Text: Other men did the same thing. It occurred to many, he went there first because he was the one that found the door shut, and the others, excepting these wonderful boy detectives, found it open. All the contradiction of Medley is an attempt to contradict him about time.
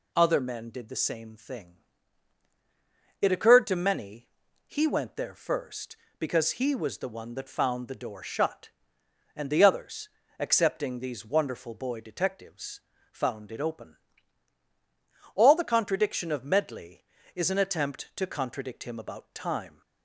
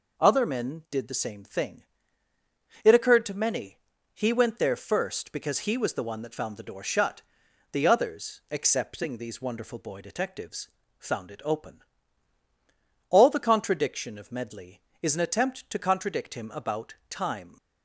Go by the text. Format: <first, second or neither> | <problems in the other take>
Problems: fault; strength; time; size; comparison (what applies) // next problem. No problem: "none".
first | skips "and"; at 7.4 s // pauses between "about" and "time"; slight; at 16.9 s; 0.16 s long